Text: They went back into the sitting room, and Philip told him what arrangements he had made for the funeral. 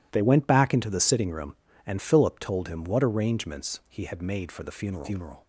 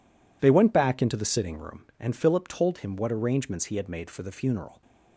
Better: second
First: says "funeral" twice; at 5.0 s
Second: none

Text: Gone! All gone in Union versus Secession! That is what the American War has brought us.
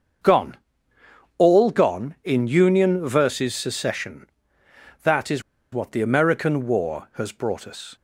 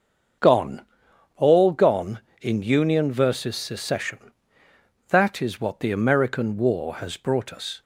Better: second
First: starts louder than the rest; until 2.0 s; 6.5 dB // pauses between "is" and "what"; slight; at 5.4 s; 0.30 s long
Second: starts louder than the rest; until 1.8 s; 6.5 dB

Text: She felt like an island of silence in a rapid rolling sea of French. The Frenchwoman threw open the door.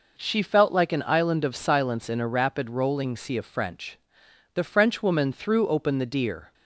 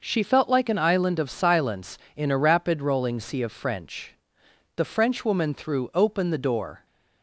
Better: second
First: says "deer" for "door"; at 6.0 s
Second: none

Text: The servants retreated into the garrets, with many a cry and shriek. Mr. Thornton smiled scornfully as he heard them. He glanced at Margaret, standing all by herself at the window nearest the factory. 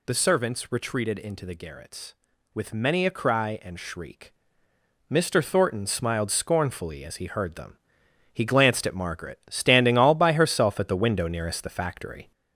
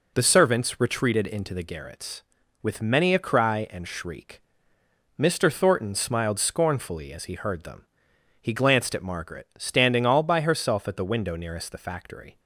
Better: second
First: gets louder; noticeable; throughout; 4.5 dB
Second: none

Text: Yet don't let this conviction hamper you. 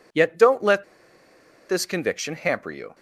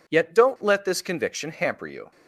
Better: second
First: pauses between "let" and "this"; noticeable; at 0.8 s; 0.84 s long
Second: none

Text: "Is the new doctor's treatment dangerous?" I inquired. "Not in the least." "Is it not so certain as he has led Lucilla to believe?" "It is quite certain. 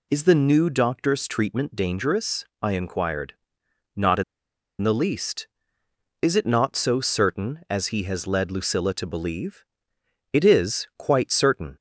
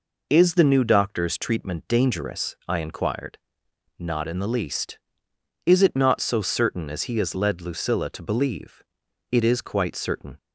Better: second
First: pauses between "in" and "the"; noticeable; at 4.2 s; 0.58 s long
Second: none

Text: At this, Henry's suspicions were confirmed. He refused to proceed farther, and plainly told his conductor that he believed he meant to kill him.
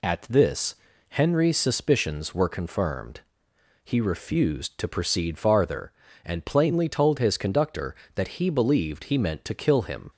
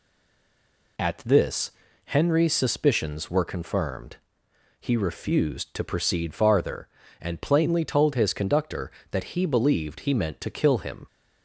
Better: first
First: none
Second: stays silent before the first word; until 0.9 s; 0.9 s long

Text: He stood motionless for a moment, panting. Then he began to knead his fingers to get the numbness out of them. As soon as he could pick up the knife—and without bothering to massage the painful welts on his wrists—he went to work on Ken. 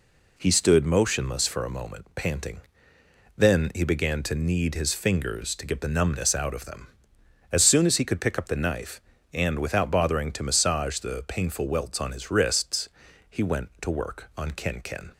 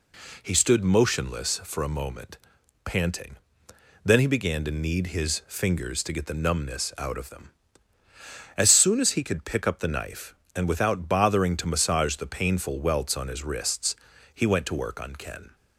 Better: second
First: says "Ken" twice; at 14.8 s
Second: none

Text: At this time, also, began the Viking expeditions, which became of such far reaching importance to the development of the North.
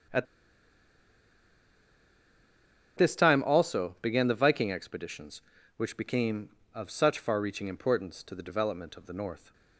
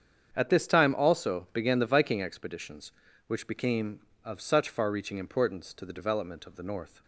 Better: second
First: starts louder than the rest; strong; until 3.8 s; 8 dB // pauses between "At" and "this"; strong; at 0.2 s; 2.7 s long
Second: starts louder than the rest; strong; until 1.3 s; 7.5 dB

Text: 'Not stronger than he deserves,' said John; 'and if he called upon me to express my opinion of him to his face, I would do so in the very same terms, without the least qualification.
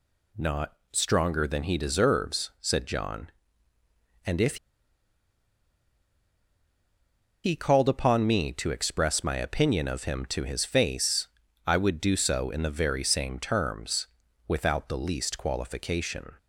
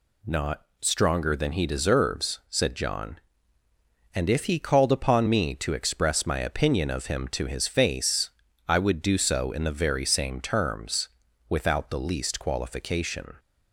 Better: second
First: pauses between "Not" and "stronger"; slight; at 0.7 s; 0.16 s long // pauses between "if" and "he"; strong; at 4.5 s; 2.8 s long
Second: pauses between "Not" and "stronger"; slight; at 0.6 s; 0.16 s long

